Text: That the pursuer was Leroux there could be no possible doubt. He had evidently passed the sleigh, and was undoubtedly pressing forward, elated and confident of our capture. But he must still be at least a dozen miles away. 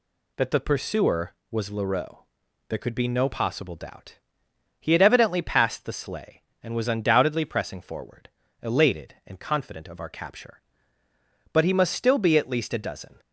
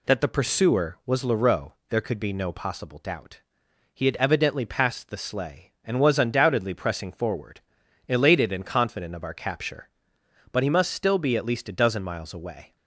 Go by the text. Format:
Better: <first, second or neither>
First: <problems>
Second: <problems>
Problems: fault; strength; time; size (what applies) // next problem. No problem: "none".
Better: second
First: pauses between "Leroux" and "there"; noticeable; at 2.1 s; 0.52 s long // stops before "miles away"; at 13.1 s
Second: pauses between "Leroux" and "there"; slight; at 1.7 s; 0.18 s long